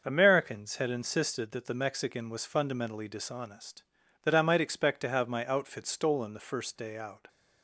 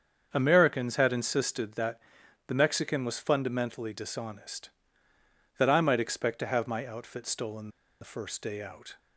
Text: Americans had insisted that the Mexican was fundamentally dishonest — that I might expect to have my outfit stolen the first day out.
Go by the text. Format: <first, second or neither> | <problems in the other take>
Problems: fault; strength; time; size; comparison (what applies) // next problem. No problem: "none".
first | starts louder than the rest; until 1.3 s; 7 dB; noticeable in the first // pauses between "that" and "the"; noticeable; at 1.9 s; 0.50 s long // pauses between "stolen" and "the"; slight; at 7.6 s; 0.31 s long